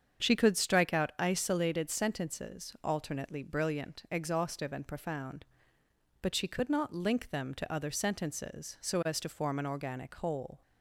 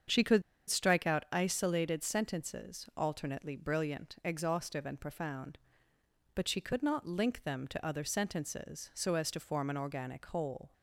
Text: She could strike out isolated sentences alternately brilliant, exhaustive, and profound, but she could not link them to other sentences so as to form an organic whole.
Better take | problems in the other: first | starts louder than the rest; strong; until 1.4 s; 7.5 dB; strong in the first // pauses between "could" and "strike"; slight; at 0.4 s; 0.26 s long

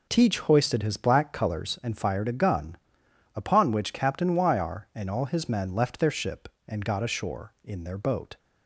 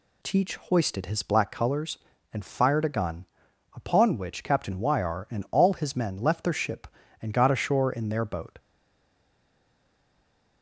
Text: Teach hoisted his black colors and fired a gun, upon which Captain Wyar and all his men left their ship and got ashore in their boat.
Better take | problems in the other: first | stays silent after the last word; noticeable; from 8.5 s on; 2.1 s long

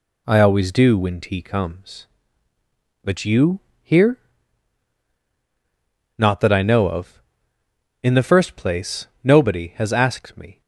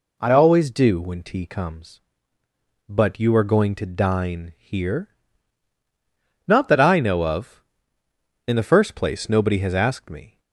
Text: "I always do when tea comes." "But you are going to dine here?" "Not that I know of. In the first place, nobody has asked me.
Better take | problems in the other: second | skips "are going to dine"; at 3.7 s

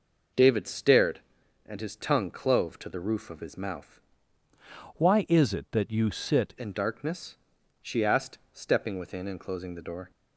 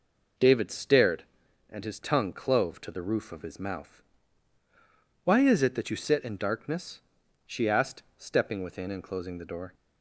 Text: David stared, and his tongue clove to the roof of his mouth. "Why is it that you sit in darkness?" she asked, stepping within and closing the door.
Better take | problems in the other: second | changes voice from "Why" to "sit"; from 4.9 to 6.5 s; 1.6 s long

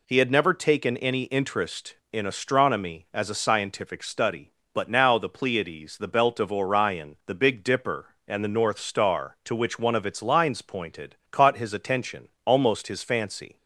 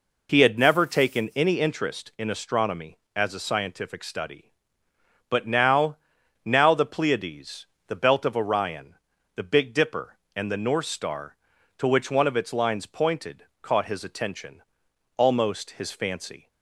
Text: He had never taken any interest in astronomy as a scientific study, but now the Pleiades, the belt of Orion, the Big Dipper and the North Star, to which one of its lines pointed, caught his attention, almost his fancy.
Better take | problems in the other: first | says "now" twice; at 6.4 s

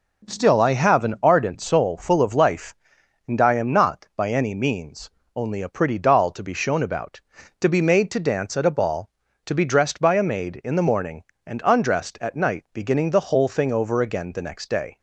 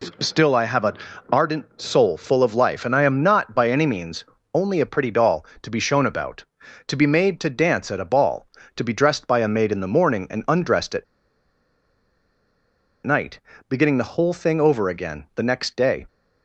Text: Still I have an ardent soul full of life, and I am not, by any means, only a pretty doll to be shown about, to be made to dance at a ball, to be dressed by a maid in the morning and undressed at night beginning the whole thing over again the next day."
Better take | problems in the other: first | pauses between "an" and "ardent"; slight; at 0.9 s; 0.34 s long // pauses between "at" and "night"; strong; at 11.0 s; 1.9 s long // pauses between "night" and "beginning"; slight; at 13.3 s; 0.30 s long

